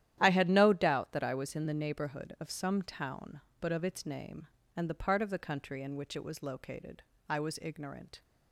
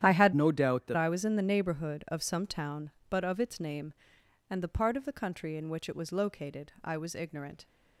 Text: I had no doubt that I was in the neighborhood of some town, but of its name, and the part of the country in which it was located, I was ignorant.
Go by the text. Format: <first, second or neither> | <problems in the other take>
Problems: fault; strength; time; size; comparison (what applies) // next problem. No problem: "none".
first | starts louder than the rest; strong; until 1.0 s; 10.5 dB; strong in the first // changes voice from "no" to "that"; from 0.3 to 0.9 s; 0.6 s long